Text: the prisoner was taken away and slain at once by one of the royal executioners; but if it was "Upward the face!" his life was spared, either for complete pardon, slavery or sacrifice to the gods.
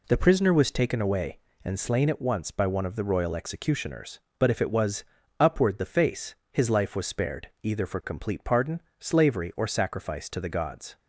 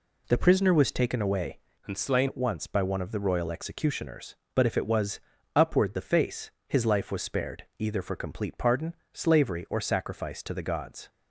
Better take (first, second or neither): first